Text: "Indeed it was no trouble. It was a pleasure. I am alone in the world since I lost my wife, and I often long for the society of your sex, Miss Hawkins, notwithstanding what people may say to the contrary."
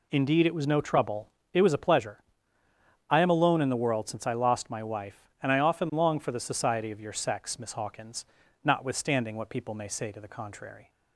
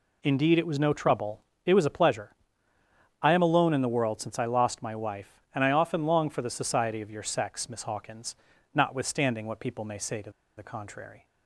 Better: first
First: none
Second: pauses between "to" and "the"; slight; at 10.3 s; 0.27 s long

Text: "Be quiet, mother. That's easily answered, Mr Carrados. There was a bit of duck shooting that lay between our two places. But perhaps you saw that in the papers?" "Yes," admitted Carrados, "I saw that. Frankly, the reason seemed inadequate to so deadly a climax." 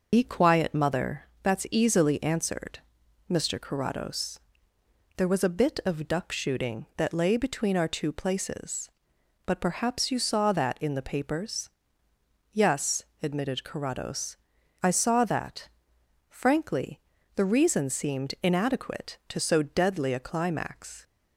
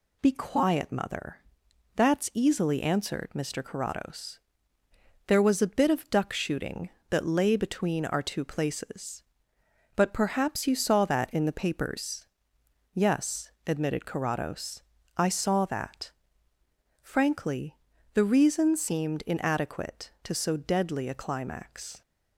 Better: second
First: loses the start of "Be"; at 0.1 s; 80 ms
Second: none

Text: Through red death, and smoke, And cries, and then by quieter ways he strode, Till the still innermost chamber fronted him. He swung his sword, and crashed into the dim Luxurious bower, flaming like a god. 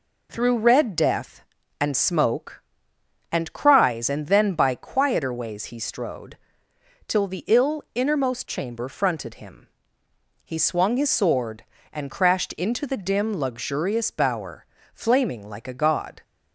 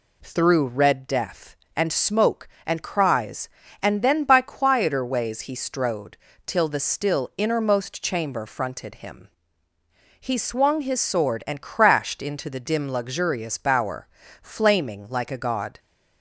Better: second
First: says "ill" for "still"; at 7.4 s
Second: none

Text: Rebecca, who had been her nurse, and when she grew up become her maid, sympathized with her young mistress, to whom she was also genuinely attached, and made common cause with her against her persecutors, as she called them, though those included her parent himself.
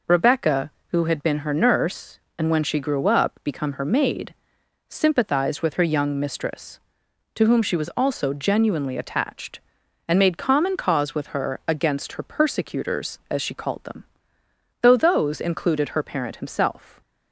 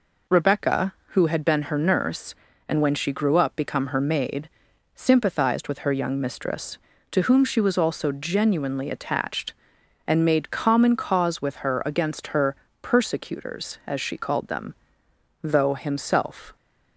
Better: first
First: none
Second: pauses between "her" and "persecutors"; slight; at 12.5 s; 0.26 s long // skips "those included her parent"; at 15.7 s

